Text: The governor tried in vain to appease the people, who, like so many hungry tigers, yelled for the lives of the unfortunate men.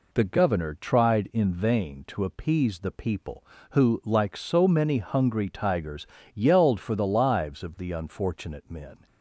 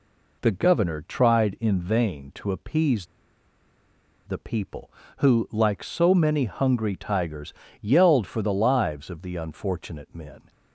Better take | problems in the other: first | pauses between "appease" and "the"; at 3.0 s; 1.1 s long

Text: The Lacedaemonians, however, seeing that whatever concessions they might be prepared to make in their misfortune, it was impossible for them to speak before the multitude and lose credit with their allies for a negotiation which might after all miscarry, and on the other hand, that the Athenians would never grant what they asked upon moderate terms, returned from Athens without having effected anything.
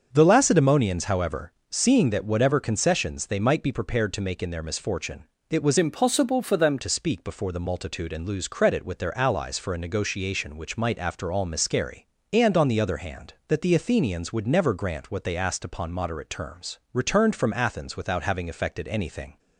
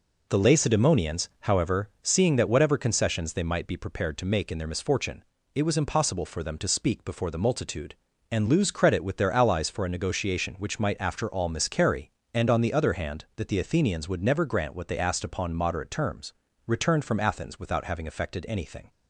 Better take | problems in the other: second | starts louder than the rest; strong; until 1.1 s; 7 dB // changes voice from "impossible" to "them"; from 5.7 to 6.7 s; 1.0 s long

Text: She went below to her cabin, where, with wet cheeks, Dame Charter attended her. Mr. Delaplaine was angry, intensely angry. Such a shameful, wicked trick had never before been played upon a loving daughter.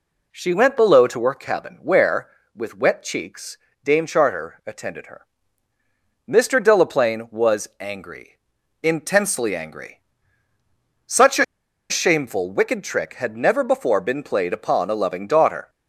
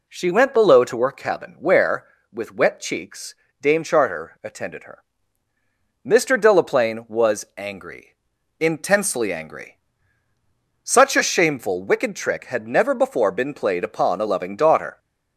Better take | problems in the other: second | pauses between "a" and "shameful"; noticeable; at 11.4 s; 0.46 s long

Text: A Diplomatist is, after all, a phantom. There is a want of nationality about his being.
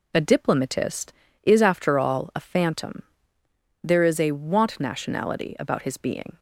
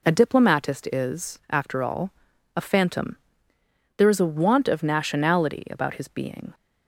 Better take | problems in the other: second | skips "of"; at 4.8 s

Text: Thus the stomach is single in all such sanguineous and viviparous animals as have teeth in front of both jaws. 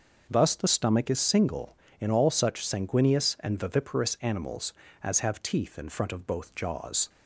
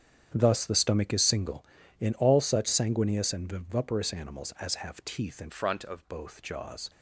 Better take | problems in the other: first | starts louder than the rest; strong; until 1.3 s; 8.5 dB; also in the first // changes voice from "front" to "of"; from 5.4 to 6.0 s; 0.6 s long

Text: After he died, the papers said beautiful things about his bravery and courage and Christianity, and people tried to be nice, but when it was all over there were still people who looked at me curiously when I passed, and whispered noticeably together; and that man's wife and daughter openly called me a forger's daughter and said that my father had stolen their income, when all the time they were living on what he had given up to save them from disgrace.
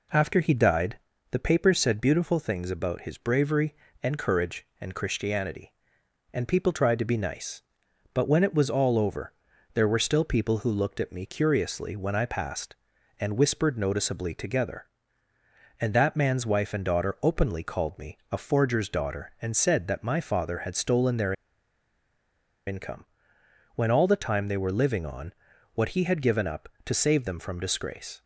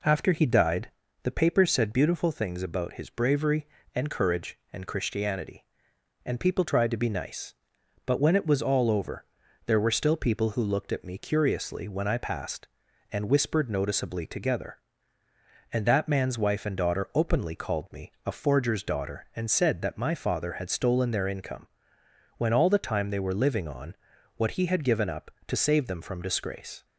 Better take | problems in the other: second | pauses between "over" and "there"; at 9.3 s; 0.42 s long; also in the second // pauses between "their" and "income"; strong; at 21.3 s; 1.3 s long // pauses between "on" and "what"; at 25.3 s; 0.42 s long; also in the second

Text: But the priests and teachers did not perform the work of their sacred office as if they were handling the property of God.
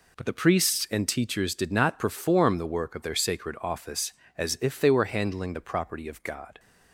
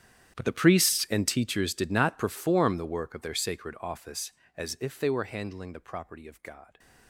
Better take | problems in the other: first | gets quieter; strong; throughout; 19.5 dB

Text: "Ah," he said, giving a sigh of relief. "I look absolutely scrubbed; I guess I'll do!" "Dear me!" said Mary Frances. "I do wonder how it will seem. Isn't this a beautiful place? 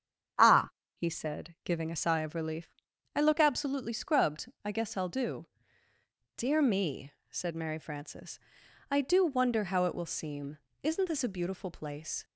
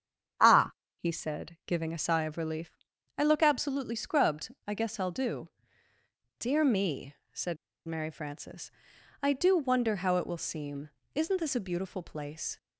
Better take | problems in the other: first | starts louder than the rest; strong; until 1.7 s; 8 dB; strong in the first // pauses between "said" and "Mary"; slight; at 7.5 s; 0.31 s long

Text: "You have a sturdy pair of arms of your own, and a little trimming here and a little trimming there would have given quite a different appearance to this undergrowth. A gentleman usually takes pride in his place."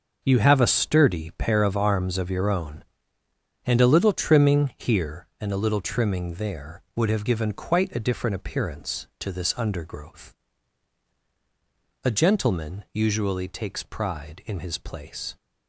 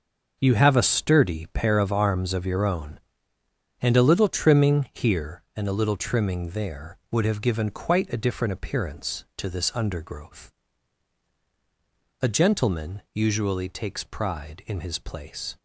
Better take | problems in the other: neither | starts louder than the rest; noticeable; the same in both

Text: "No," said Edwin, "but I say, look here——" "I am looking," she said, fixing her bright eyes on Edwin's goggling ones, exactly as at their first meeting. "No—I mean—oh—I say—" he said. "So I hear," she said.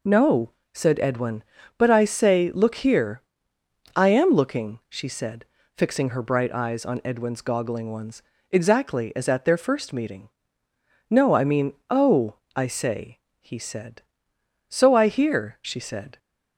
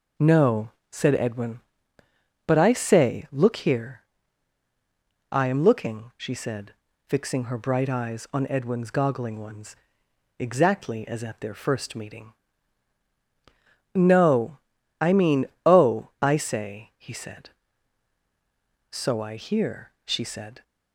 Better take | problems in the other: neither | none

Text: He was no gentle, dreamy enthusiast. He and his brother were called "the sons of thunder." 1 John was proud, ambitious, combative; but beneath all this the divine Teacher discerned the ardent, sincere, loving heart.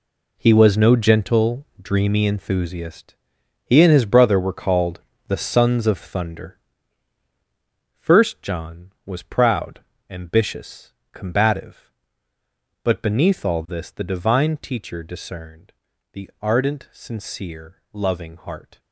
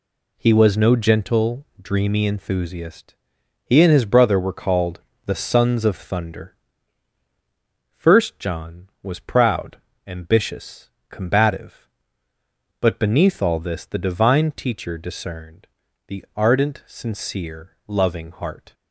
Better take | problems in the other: second | gets quieter; strong; throughout; 11 dB // pauses between "called" and "the"; slight; at 5.0 s; 0.28 s long; slight in the second // pauses between "discerned" and "the"; at 15.7 s; 0.40 s long; also in the second

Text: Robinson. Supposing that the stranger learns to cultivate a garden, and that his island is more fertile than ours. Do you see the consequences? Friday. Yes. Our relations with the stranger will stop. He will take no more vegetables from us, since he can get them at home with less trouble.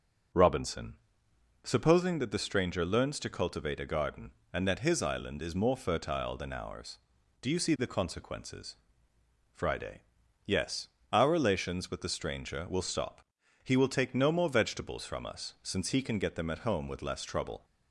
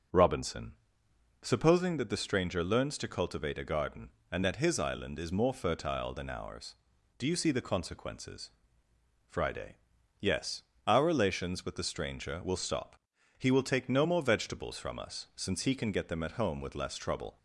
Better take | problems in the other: neither | starts louder than the rest; the same in both

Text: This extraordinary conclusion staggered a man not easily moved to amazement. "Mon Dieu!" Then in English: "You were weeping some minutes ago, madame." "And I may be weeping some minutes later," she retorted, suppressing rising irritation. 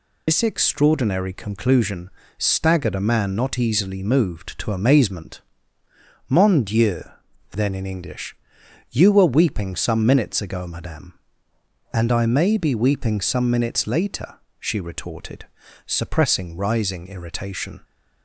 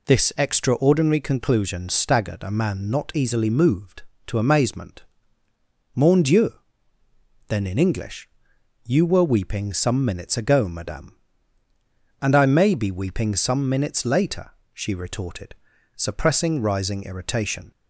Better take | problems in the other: second | loses the start of "This"; at 0.2 s; 105 ms // pauses between "conclusion" and "staggered"; slight; at 2.1 s; 0.28 s long

